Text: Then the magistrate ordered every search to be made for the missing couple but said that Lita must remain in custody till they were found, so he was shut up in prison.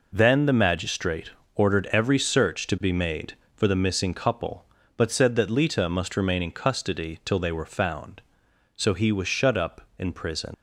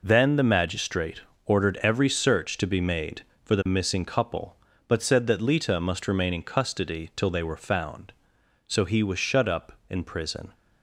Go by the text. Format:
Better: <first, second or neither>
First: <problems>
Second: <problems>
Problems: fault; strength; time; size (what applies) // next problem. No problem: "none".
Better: second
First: pauses between "magistrate" and "ordered"; slight; at 1.3 s; 0.24 s long // leaves "prison" unfinished; at 10.5 s; 80 ms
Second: pauses between "magistrate" and "ordered"; slight; at 1.2 s; 0.24 s long